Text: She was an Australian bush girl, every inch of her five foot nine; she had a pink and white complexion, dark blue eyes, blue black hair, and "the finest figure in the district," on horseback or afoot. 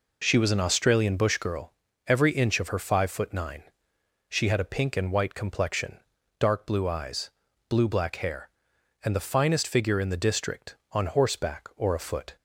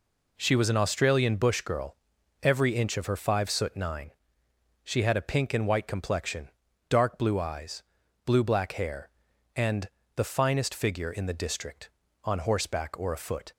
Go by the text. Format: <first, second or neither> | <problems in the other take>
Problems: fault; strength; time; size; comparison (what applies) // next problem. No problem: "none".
first | says "soot" for "foot"; at 3.4 s // pauses between "and" and "the"; slight; at 9.8 s; 0.26 s long